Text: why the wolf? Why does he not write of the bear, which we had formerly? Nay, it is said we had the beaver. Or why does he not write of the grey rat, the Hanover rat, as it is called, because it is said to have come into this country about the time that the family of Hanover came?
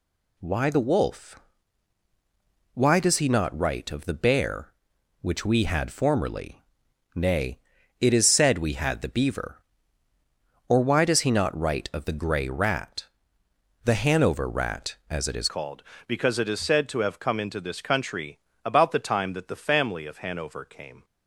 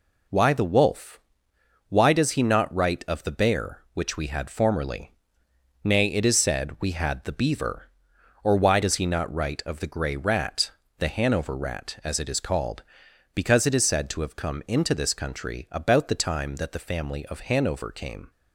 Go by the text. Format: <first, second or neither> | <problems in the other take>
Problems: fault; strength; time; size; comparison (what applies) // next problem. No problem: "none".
second | changes voice at "called"; from 15.4 s on; 5.6 s long // pauses between "country" and "about"; slight; at 18.3 s; 0.26 s long